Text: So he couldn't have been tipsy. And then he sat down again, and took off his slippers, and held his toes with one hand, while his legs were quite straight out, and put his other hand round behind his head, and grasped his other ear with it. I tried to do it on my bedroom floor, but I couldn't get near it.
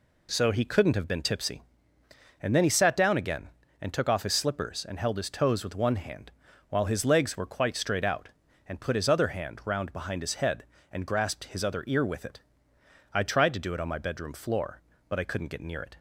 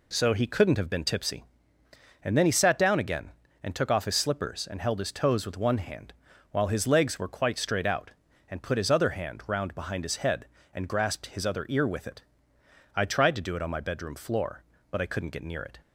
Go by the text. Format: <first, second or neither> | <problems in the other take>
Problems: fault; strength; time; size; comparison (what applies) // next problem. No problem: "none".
neither | none